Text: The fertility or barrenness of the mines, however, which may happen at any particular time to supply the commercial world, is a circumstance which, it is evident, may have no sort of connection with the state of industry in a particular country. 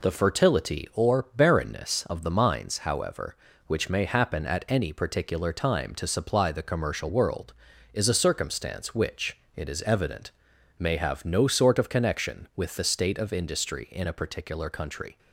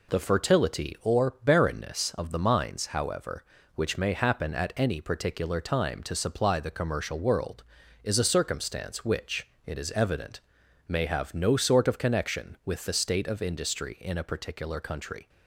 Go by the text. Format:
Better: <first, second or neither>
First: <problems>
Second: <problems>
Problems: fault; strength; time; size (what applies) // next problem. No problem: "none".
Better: neither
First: none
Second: none